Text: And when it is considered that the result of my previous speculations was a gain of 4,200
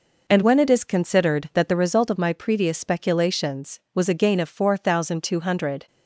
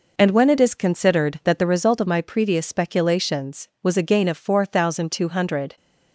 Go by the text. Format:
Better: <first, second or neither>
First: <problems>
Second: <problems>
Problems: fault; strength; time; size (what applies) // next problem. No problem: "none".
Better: neither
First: none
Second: none